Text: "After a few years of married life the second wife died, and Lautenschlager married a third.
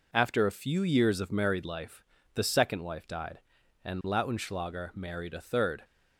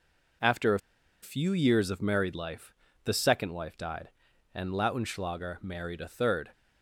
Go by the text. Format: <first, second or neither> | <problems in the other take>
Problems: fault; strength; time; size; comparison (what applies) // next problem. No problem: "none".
first | pauses between "a" and "few"; at 0.7 s; 0.43 s long // pauses between "life" and "the"; slight; at 2.7 s; 0.30 s long; slight in the first